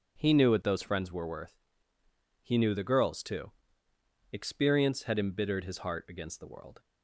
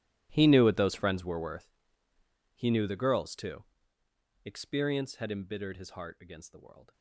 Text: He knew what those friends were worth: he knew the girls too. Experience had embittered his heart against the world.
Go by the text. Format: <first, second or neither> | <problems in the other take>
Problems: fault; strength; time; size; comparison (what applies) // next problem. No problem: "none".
first | gets quieter; strong; throughout; 19 dB